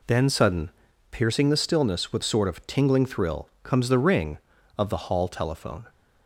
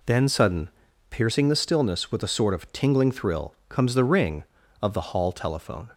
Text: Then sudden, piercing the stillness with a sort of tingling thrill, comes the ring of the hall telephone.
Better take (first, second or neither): second